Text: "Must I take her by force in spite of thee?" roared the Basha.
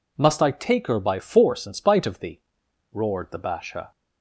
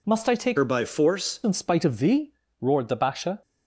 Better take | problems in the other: first | changes voice from "her" to "force"; from 0.5 to 1.3 s; 0.8 s long

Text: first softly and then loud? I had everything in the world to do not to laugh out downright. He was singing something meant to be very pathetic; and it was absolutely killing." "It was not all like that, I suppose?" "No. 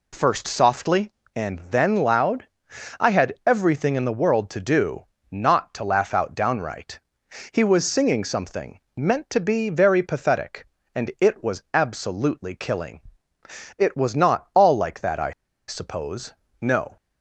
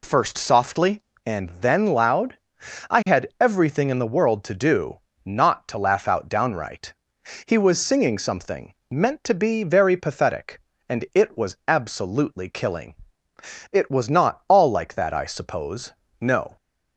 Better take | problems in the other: second | pauses between "do" and "not"; slight; at 5.0 s; 0.26 s long; slight in the second // pauses between "something" and "meant"; slight; at 8.7 s; 0.16 s long; slight in the second // pauses between "I" and "suppose"; at 15.3 s; 0.36 s long

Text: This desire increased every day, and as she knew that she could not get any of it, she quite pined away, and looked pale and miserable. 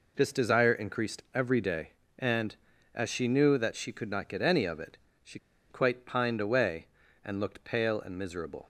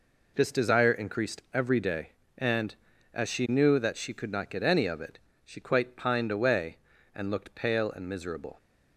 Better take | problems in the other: second | pauses between "she" and "quite"; slight; at 5.3 s; 0.32 s long

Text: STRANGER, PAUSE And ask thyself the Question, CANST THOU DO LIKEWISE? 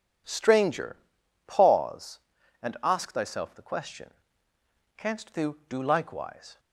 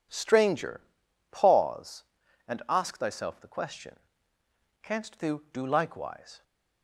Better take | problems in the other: neither | none

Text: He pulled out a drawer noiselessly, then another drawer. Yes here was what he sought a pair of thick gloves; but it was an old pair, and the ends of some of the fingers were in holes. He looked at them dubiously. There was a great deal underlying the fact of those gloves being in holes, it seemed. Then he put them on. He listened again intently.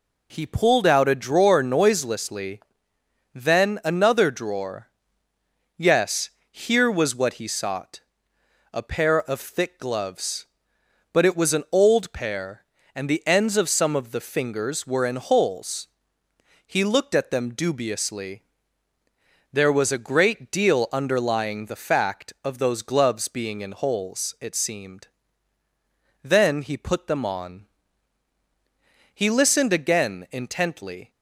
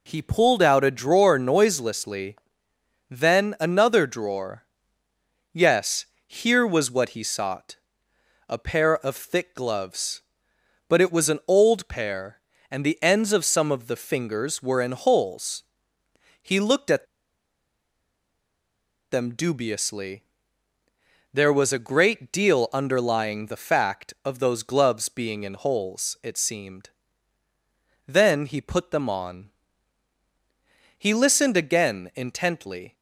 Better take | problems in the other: first | pauses between "Yes" and "here"; slight; at 6.0 s; 0.20 s long; slight in the first // pauses between "sought" and "a"; noticeable; at 7.7 s; 0.72 s long; noticeable in the first // pauses between "at" and "them"; strong; at 17.0 s; 2.0 s long

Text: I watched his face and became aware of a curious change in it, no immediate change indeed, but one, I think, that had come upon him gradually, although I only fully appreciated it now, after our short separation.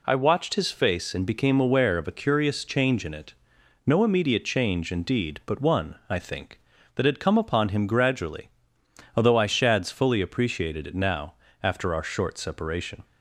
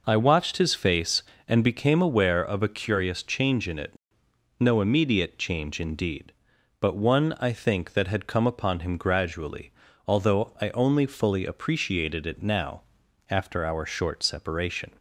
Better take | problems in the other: second | says "shads" for "only"; at 9.4 s

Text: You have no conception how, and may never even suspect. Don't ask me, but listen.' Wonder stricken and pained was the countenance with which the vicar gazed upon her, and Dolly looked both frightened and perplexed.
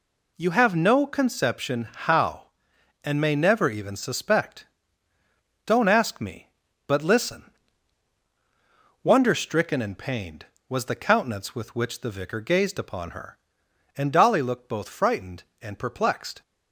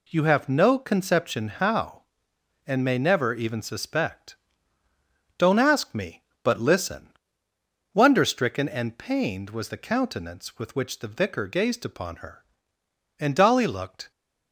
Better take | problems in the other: first | stops before "both frightened and perplexed"; at 14.1 s

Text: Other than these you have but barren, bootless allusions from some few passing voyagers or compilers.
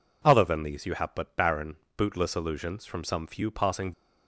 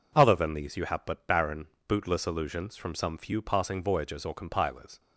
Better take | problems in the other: second | stops before "voyagers or compilers"; at 3.9 s

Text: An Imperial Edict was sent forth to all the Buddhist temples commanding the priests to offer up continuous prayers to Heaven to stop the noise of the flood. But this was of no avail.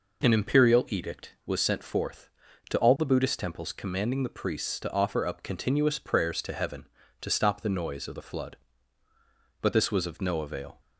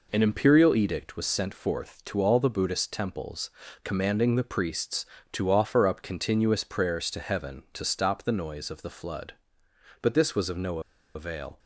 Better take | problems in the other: first | pauses between "temples" and "commanding"; slight; at 3.5 s; 0.32 s long // pauses between "no" and "avail"; slight; at 10.7 s; 0.35 s long

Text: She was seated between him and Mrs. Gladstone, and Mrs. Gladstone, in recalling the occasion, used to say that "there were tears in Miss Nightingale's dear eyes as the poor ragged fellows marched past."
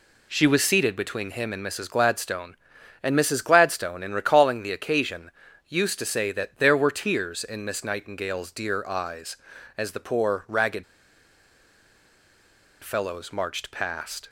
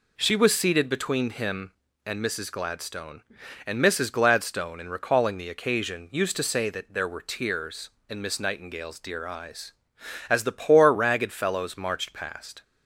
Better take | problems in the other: second | pauses between "ragged" and "fellows"; strong; at 10.8 s; 1.9 s long

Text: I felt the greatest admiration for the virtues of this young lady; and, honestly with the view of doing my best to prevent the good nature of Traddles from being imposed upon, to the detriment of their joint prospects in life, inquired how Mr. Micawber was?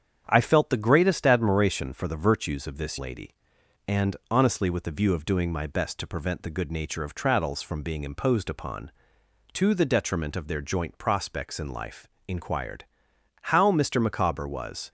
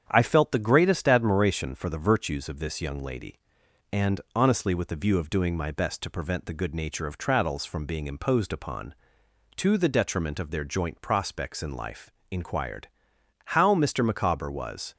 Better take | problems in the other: second | starts louder than the rest; strong; until 1.2 s; 8 dB; strong in the second // skips "young"; at 2.9 s // pauses between "inquired" and "how"; noticeable; at 12.8 s; 0.56 s long; noticeable in the second

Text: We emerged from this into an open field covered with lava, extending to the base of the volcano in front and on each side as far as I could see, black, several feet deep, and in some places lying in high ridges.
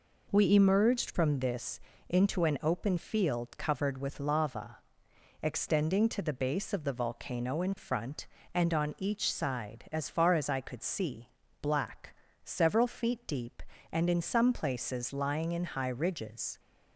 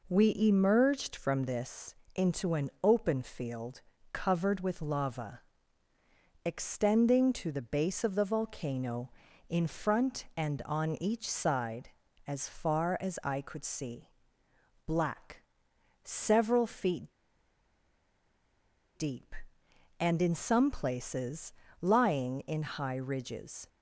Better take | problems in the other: first | pauses between "this" and "into"; slight; at 1.9 s; 0.20 s long; slight in the first // pauses between "field" and "covered"; slight; at 3.7 s; 0.32 s long // pauses between "feet" and "deep"; strong; at 17.1 s; 1.8 s long // pauses between "places" and "lying"; slight; at 21.5 s; 0.26 s long

